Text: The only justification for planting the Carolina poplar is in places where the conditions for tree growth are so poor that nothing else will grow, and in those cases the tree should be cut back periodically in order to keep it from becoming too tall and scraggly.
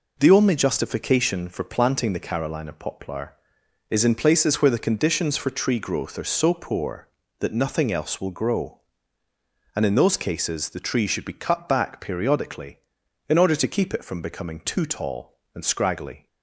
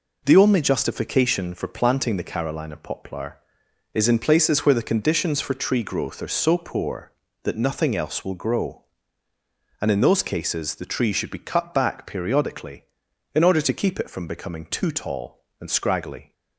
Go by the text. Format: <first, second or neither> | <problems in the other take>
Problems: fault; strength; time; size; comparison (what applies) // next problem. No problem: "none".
neither | none